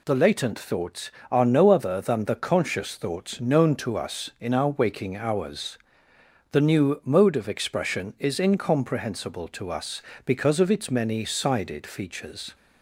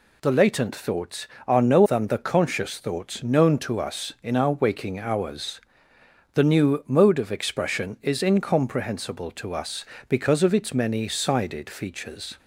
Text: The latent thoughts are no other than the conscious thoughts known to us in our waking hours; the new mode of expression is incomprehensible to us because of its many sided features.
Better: first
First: none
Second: skips "other"; at 1.8 s

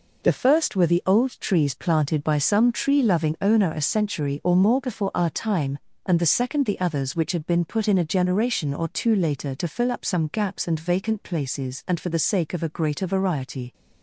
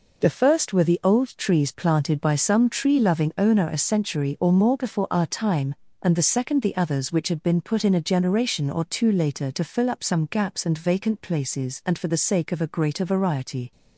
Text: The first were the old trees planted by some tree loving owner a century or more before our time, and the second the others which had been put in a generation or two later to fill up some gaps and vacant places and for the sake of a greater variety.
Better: neither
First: none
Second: none

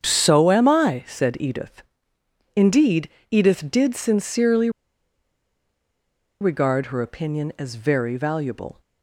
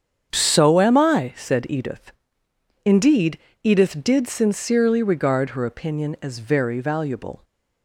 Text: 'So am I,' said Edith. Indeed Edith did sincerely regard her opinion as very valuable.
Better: second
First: starts louder than the rest; strong; until 1.0 s; 7.5 dB // pauses between "Indeed" and "Edith"; slight; at 3.0 s; 0.22 s long // pauses between "sincerely" and "regard"; strong; at 4.6 s; 1.7 s long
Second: starts louder than the rest; strong; until 1.3 s; 7.5 dB // pauses between "Indeed" and "Edith"; slight; at 3.3 s; 0.25 s long

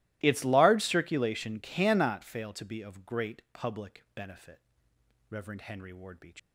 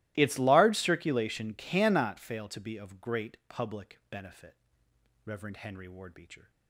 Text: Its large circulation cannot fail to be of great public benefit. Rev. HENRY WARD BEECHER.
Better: second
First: starts louder than the rest; strong; until 1.2 s; 18 dB // leaves "BEECHER" unfinished; at 6.3 s; 170 ms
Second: starts louder than the rest; strong; until 1.1 s; 18 dB

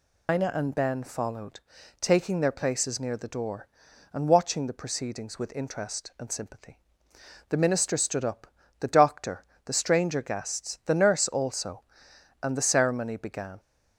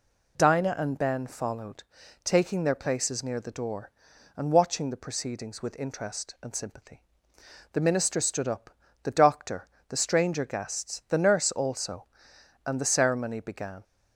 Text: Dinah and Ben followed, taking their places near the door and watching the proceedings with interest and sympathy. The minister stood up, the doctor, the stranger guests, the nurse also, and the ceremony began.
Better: second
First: loses the start of "Dinah"; at 0.2 s; 155 ms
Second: none

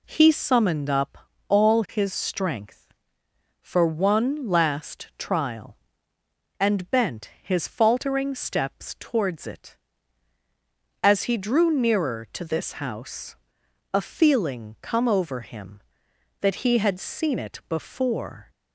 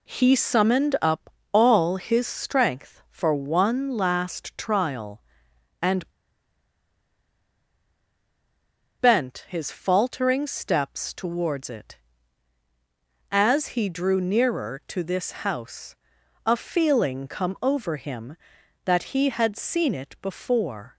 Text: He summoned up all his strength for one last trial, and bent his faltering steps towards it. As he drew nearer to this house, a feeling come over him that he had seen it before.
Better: first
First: pauses between "up" and "all"; slight; at 1.1 s; 0.32 s long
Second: pauses between "up" and "all"; slight; at 1.2 s; 0.22 s long // pauses between "and" and "bent"; strong; at 6.0 s; 2.9 s long

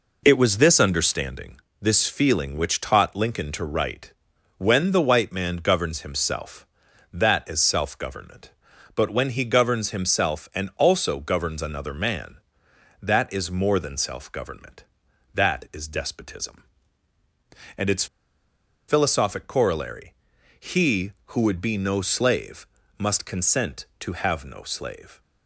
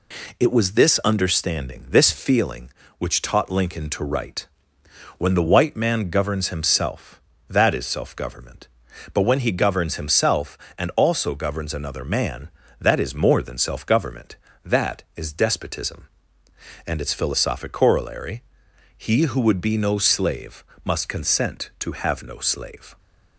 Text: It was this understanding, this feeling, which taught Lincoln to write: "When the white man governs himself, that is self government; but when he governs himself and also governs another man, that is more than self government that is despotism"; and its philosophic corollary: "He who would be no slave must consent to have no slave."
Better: second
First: pauses between "its" and "philosophic"; noticeable; at 18.0 s; 0.82 s long // pauses between "slave" and "must"; slight; at 22.6 s; 0.32 s long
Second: pauses between "slave" and "must"; slight; at 20.6 s; 0.20 s long

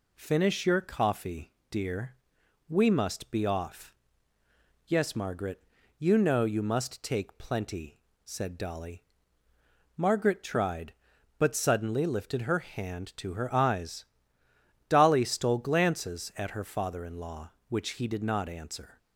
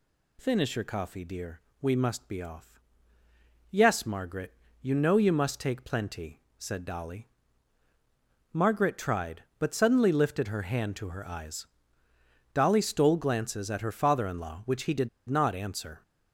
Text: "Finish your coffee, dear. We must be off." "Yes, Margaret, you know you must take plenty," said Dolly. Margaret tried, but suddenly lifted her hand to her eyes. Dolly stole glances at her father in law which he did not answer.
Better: first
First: none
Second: pauses between "did" and "not"; slight; at 15.0 s; 0.20 s long

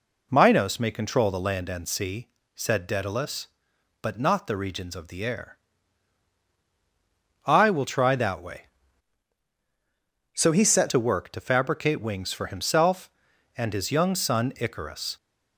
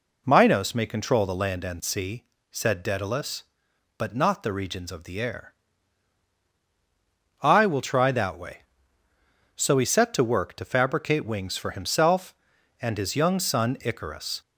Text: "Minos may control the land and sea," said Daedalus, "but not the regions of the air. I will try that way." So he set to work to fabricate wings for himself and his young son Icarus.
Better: second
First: changes voice from "So" to "set"; from 10.3 to 10.8 s; 0.5 s long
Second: none

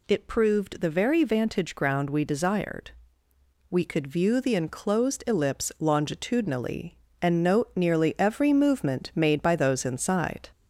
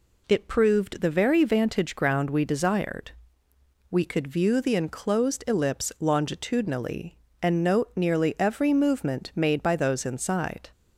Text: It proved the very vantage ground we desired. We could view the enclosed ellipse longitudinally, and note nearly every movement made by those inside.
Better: second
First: gets louder; slight; throughout; 2.5 dB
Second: none

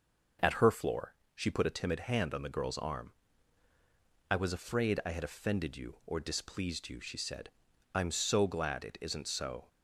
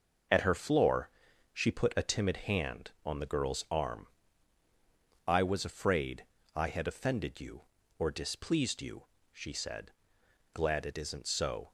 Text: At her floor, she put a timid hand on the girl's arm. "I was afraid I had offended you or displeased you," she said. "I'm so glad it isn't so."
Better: first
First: none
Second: pauses between "afraid" and "I"; slight; at 6.2 s; 0.32 s long // skips "I'm so"; at 10.2 s

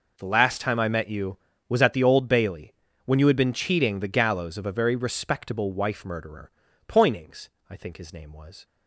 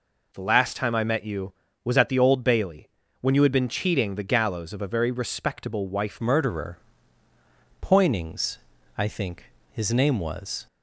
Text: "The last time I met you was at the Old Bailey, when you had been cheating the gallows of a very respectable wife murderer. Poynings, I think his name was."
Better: first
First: none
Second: changes voice at "murderer"; from 6.2 s on; 4.4 s long // pauses between "think" and "his"; slight; at 9.4 s; 0.28 s long

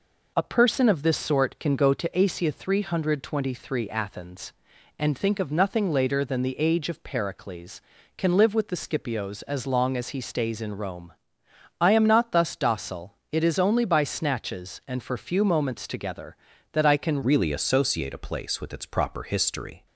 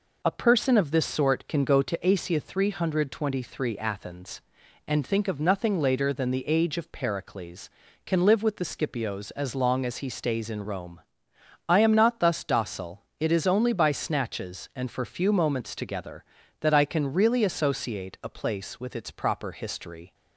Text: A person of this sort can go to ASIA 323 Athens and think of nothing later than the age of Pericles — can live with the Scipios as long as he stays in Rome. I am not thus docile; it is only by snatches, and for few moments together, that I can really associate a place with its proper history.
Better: second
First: changes voice at "really"; from 17.2 s on; 2.6 s long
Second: none

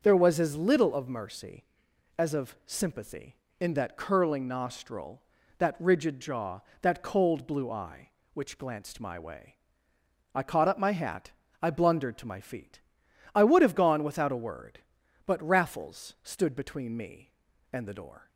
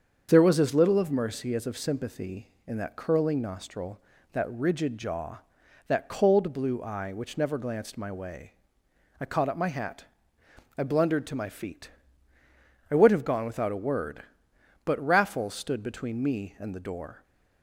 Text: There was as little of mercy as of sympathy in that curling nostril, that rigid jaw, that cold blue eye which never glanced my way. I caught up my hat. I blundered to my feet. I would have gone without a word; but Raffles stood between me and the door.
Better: second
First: starts louder than the rest; until 1.0 s; 6.5 dB // skips "never"; at 8.5 s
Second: starts louder than the rest; until 1.3 s; 7 dB

